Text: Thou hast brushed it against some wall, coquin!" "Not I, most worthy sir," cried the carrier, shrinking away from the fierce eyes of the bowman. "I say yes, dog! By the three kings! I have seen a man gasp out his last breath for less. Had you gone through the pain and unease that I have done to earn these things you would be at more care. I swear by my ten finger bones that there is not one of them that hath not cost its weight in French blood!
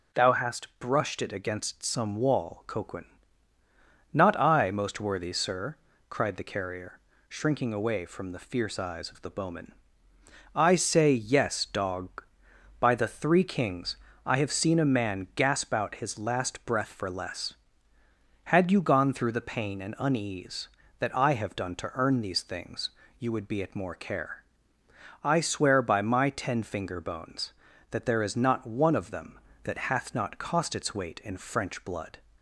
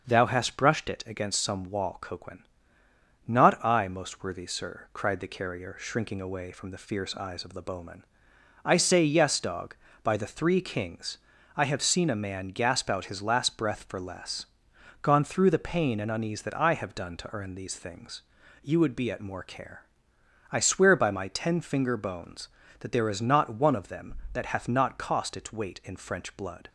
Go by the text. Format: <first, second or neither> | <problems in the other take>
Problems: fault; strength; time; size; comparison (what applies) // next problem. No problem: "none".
first | starts louder than the rest; until 1.1 s; 6 dB // skips "Had you"; at 14.7 s // pauses between "things" and "you"; at 18.2 s; 0.42 s long; slight in the first